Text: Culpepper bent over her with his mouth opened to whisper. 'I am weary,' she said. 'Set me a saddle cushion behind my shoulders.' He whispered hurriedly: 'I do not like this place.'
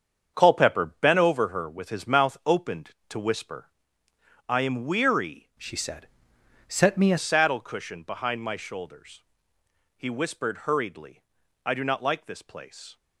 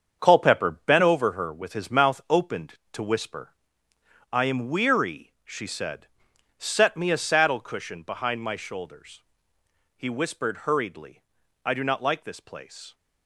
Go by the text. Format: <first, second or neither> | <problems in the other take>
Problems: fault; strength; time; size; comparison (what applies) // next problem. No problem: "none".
second | starts louder than the rest; strong; until 1.3 s; 7 dB; strong in the second // changes voice from "she" to "a"; from 5.5 to 7.1 s; 1.6 s long